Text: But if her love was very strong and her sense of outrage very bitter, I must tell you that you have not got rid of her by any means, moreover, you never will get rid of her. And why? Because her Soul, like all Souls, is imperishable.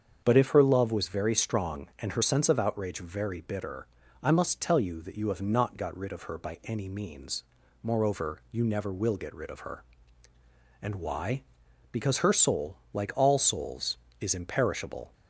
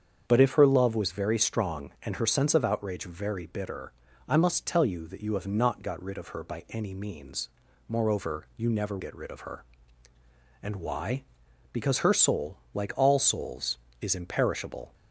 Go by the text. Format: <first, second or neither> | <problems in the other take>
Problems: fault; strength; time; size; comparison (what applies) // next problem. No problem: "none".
first | starts louder than the rest; strong; until 1.2 s; 7.5 dB; strong in the first // skips "will"; at 8.9 s